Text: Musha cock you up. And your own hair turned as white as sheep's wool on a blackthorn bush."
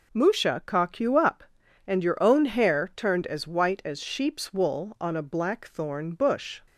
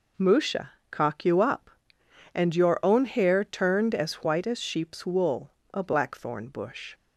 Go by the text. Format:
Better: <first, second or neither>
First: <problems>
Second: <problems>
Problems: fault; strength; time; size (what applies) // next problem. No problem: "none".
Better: first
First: none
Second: pauses between "Musha" and "cock"; slight; at 0.7 s; 0.22 s long // skips "on"; at 5.6 s